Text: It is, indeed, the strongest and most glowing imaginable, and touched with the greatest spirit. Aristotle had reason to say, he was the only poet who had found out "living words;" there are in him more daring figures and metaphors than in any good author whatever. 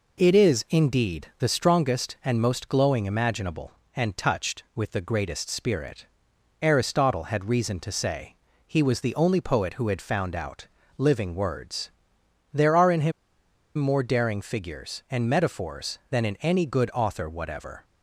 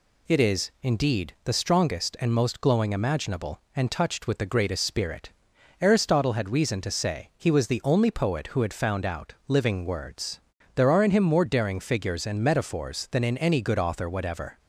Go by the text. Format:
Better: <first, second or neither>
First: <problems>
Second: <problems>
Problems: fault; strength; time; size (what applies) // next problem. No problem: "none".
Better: second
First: pauses between "out" and "living"; slight; at 10.6 s; 0.30 s long // pauses between "him" and "more"; noticeable; at 13.1 s; 0.66 s long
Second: pauses between "out" and "living"; slight; at 9.3 s; 0.16 s long